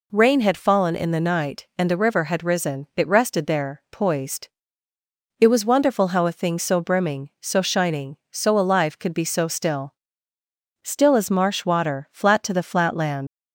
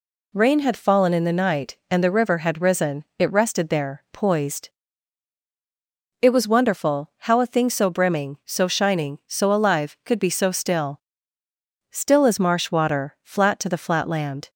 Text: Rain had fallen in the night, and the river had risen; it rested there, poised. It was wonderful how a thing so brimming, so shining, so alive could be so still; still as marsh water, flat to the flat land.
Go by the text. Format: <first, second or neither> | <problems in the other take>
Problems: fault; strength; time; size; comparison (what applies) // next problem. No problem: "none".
second | leaves "land" unfinished; at 13.2 s; 120 ms